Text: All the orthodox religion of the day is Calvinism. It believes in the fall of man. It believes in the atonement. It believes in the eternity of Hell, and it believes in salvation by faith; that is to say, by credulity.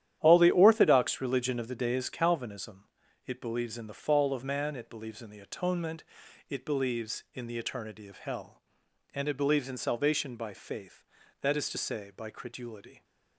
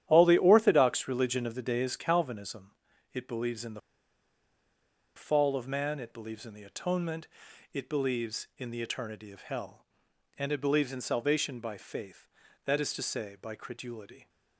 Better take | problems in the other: first | starts louder than the rest; strong; until 1.0 s; 11 dB; strong in the first // pauses between "the" and "fall"; strong; at 3.8 s; 1.3 s long

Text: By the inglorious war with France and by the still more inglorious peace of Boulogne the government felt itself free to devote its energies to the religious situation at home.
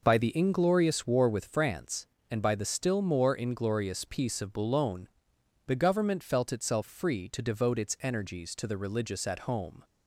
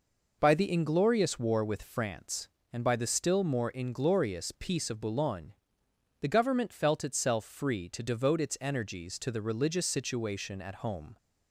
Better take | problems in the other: second | pauses between "Boulogne" and "the"; noticeable; at 5.0 s; 0.58 s long; noticeable in the second // skips "situation"; at 9.2 s

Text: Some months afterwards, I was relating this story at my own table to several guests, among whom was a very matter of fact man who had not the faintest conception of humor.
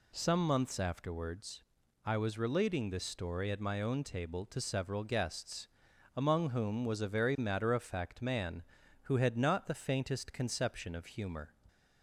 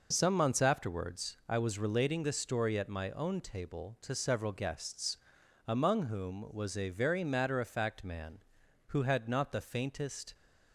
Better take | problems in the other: first | stops before "conception of humor"; at 10.3 s

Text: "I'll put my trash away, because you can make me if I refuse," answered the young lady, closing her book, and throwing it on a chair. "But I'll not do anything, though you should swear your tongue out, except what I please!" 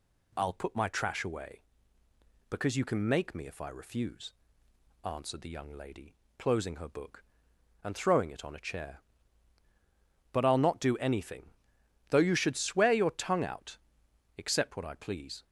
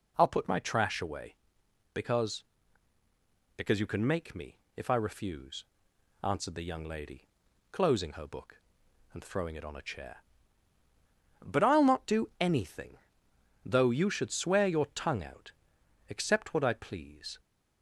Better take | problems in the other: first | says "because" twice; at 3.5 s // pauses between "me" and "if"; slight; at 4.5 s; 0.20 s long

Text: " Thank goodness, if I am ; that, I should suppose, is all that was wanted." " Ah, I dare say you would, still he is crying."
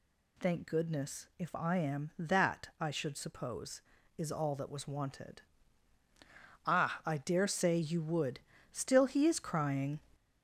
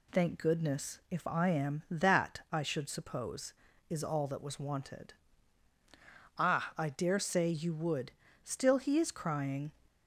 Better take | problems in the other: second | gets louder; throughout; 3.5 dB

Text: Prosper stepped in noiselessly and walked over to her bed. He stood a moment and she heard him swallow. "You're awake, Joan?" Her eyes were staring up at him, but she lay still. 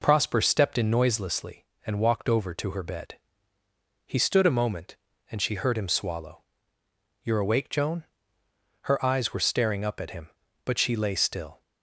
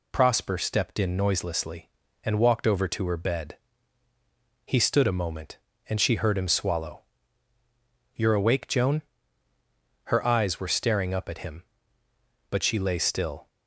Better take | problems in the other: neither | none

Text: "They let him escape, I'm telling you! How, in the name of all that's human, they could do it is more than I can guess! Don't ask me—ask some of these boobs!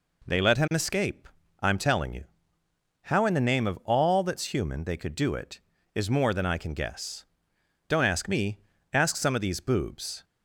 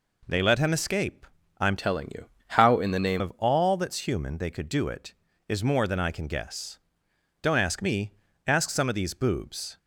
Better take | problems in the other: first | changes voice from "telling" to "name"; from 1.7 to 3.2 s; 1.5 s long

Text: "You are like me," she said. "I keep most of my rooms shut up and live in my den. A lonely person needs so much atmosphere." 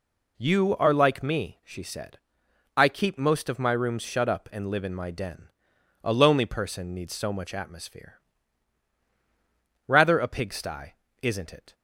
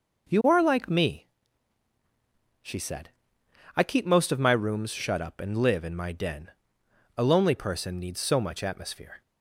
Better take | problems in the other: second | goes on to say "Rather a pigsty isn't it"; strong; from 9.8 s on; 1.8 s long

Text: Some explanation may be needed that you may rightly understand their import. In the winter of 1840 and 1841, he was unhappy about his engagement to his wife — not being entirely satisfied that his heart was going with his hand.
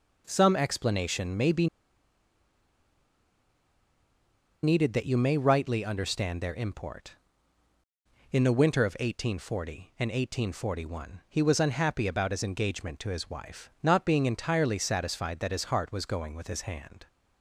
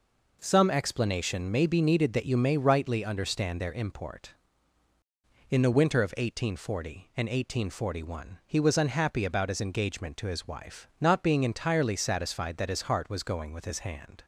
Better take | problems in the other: second | pauses between "be" and "needed"; strong; at 1.6 s; 2.9 s long

